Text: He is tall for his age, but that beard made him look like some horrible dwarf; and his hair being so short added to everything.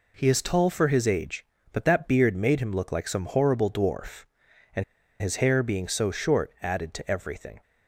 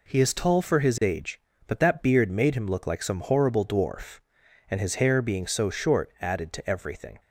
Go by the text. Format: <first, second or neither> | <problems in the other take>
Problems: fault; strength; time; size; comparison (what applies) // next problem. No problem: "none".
second | pauses between "and" and "his"; at 4.8 s; 0.37 s long